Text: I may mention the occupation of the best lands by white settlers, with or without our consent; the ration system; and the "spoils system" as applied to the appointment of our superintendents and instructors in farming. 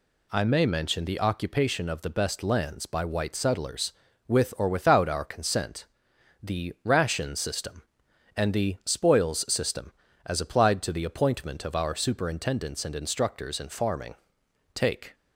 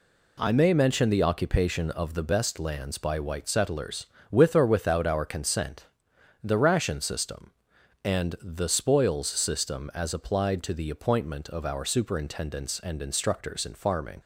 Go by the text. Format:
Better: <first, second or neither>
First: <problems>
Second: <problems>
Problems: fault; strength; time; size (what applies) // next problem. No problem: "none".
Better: second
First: goes on to say "Take"; slight; from 14.7 s on; 0.40 s long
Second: none